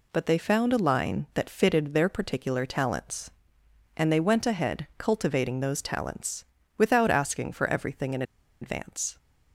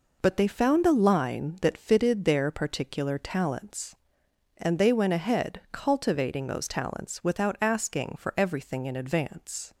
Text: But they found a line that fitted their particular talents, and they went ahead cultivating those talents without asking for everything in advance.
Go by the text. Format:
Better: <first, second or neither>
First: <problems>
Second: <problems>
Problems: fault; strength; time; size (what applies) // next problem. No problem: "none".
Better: second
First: pauses between "talents" and "without"; slight; at 6.4 s; 0.32 s long // pauses between "in" and "advance"; at 8.2 s; 0.38 s long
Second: none